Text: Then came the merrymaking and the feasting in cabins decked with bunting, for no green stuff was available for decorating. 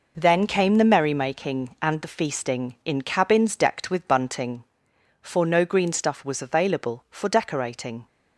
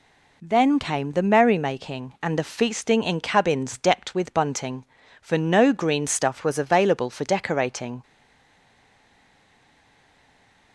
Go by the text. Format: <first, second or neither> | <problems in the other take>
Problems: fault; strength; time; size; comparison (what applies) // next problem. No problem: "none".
first | stays silent after the last word; strong; from 8.0 s on; 2.7 s long